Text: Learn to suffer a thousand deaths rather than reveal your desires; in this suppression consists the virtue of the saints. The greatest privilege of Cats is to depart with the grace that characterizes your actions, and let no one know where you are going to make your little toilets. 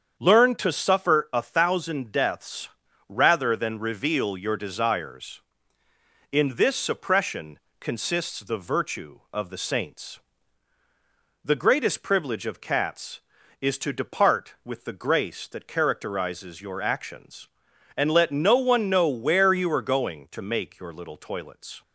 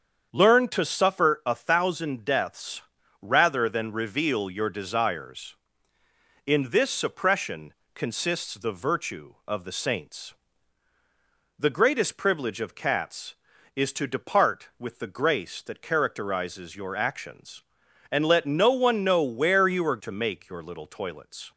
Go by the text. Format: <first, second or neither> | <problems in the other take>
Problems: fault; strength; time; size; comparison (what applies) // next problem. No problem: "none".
first | starts louder than the rest; strong; until 1.3 s; 7.5 dB; strong in the first // pauses between "deaths" and "rather"; at 2.8 s; 0.38 s long; also in the first // pauses between "suppression" and "consists"; slight; at 7.7 s; 0.22 s long; slight in the first // skips "going"; at 19.9 s